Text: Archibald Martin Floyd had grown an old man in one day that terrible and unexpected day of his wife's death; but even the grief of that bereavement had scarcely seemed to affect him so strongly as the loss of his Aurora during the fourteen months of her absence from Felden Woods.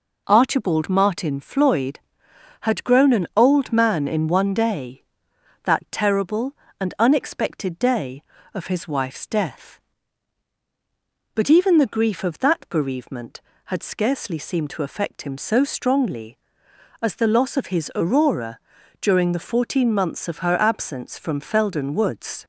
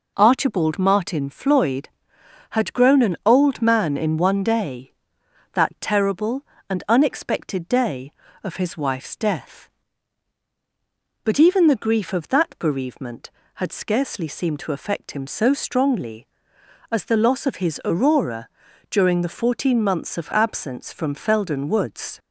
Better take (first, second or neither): first